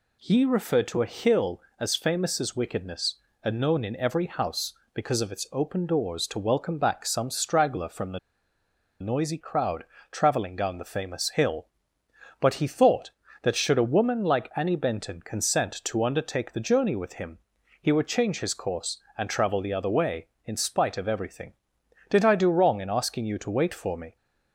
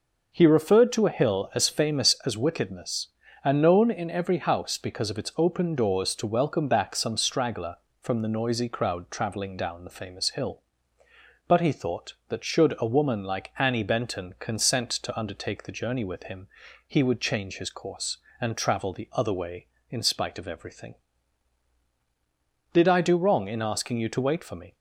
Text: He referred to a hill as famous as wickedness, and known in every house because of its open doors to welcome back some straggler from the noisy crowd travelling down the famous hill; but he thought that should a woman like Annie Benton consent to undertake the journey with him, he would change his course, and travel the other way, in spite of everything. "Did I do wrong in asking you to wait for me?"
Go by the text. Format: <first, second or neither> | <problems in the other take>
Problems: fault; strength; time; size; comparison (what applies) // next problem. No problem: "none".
second | pauses between "the" and "noisy"; noticeable; at 8.1 s; 0.82 s long // pauses between "crowd" and "travelling"; slight; at 9.8 s; 0.26 s long